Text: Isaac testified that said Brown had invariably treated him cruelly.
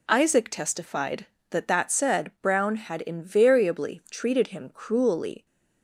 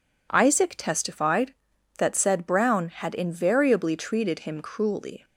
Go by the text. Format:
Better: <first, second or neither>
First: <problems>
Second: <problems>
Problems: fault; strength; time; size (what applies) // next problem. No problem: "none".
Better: second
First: says "that" twice; at 1.6 s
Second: none